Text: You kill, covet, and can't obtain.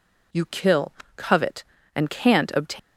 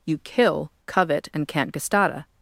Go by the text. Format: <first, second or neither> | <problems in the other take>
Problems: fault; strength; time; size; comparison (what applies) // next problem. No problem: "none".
first | says "gestata" for "obtain"; at 1.7 s